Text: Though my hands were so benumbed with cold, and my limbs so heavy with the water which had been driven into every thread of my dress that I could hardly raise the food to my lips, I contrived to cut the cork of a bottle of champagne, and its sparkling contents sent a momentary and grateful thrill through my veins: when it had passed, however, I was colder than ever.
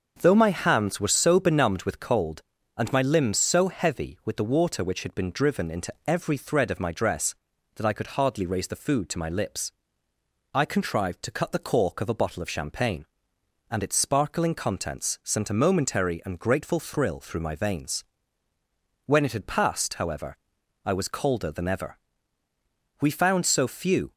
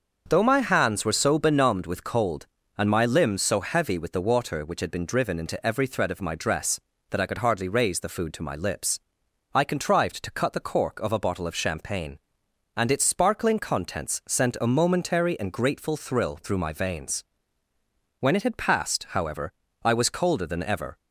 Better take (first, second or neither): second